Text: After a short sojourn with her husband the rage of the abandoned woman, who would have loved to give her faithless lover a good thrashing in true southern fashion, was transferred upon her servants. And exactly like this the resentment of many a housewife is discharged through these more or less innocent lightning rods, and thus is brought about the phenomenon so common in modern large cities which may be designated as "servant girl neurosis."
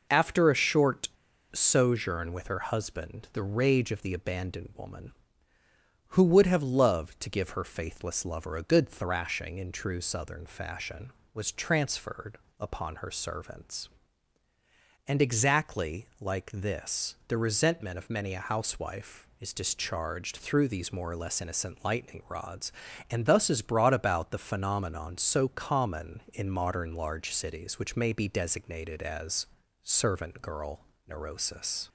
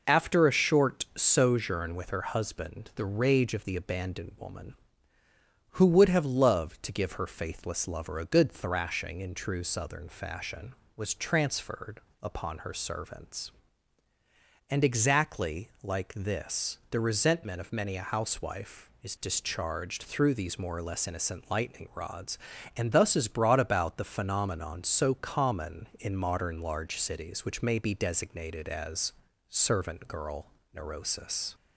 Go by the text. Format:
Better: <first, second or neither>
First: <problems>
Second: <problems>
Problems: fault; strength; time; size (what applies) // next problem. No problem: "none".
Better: second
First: pauses between "short" and "sojourn"; noticeable; at 1.0 s; 0.46 s long // pauses between "transferred" and "upon"; slight; at 12.3 s; 0.20 s long // pauses between "as" and "servant"; at 29.4 s; 0.38 s long // pauses between "girl" and "neurosis"; slight; at 30.7 s; 0.30 s long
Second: pauses between "transferred" and "upon"; slight; at 12.0 s; 0.20 s long // pauses between "as" and "servant"; at 29.1 s; 0.38 s long // pauses between "girl" and "neurosis"; slight; at 30.4 s; 0.30 s long